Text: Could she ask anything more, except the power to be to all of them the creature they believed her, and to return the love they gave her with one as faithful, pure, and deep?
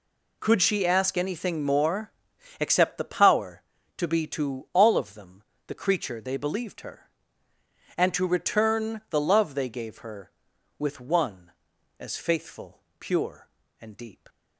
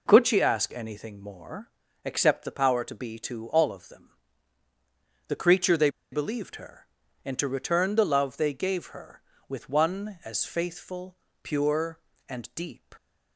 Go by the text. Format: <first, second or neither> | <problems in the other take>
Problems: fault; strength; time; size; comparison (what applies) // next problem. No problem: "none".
first | pauses between "them" and "the"; at 4.0 s; 1.1 s long; slight in the first // pauses between "they" and "believed"; slight; at 5.8 s; 0.23 s long